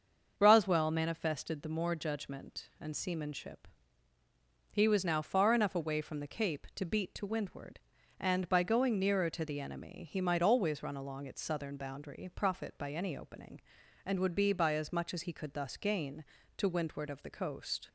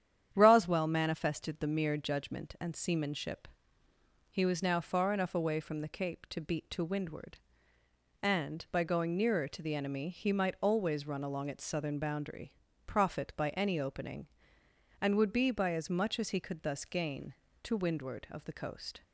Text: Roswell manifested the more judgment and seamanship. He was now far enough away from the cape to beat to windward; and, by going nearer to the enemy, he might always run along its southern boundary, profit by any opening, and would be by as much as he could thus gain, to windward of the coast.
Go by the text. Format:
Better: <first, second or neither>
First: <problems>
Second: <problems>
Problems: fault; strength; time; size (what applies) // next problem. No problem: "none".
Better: first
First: starts louder than the rest; until 1.3 s; 6.5 dB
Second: starts louder than the rest; strong; until 1.3 s; 9.5 dB // says "mere" for "more"; at 1.6 s